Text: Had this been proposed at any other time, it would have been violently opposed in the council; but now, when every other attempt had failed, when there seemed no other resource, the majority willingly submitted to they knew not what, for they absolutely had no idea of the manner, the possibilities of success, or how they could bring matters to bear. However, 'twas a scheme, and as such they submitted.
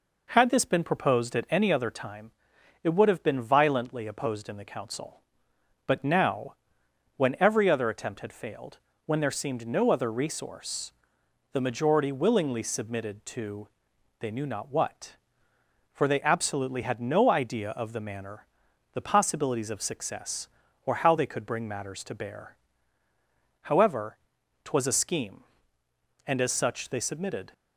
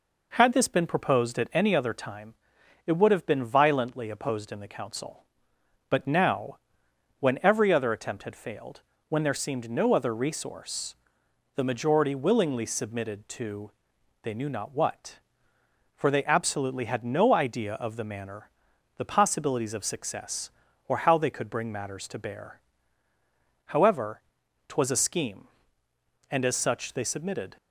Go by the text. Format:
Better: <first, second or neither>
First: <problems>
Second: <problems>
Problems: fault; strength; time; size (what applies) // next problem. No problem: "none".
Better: neither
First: pauses between "to" and "they"; noticeable; at 13.6 s; 0.50 s long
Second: pauses between "to" and "they"; noticeable; at 13.7 s; 0.50 s long